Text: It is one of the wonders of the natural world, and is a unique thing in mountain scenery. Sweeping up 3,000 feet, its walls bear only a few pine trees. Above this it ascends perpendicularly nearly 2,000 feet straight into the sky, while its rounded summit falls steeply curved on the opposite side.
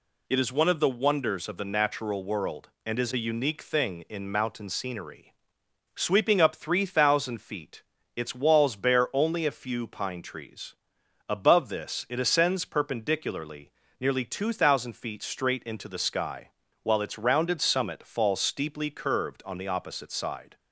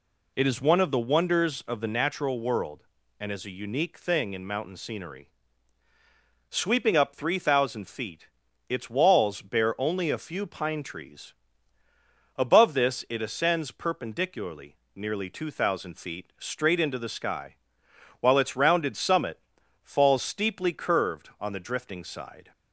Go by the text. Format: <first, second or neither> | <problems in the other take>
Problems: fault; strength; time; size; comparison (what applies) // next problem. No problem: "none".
first | pauses between "perpendicularly" and "nearly"; slight; at 14.7 s; 0.20 s long; slight in the first // pauses between "summit" and "falls"; at 19.3 s; 0.44 s long // says "drifting" for "opposite"; at 21.5 s